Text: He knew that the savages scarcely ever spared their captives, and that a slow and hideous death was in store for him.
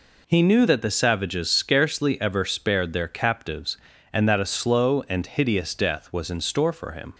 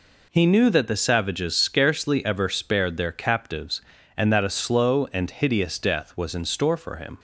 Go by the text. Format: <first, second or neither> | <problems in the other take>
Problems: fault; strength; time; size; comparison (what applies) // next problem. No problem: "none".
neither | none